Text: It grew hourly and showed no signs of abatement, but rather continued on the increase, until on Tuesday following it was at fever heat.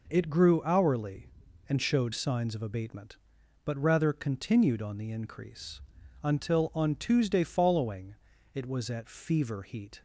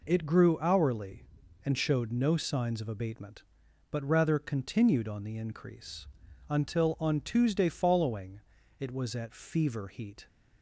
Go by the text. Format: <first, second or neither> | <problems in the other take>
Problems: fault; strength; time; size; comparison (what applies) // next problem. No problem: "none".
second | skips "no"; at 2.1 s // pauses between "following" and "it"; at 8.1 s; 0.38 s long; also in the second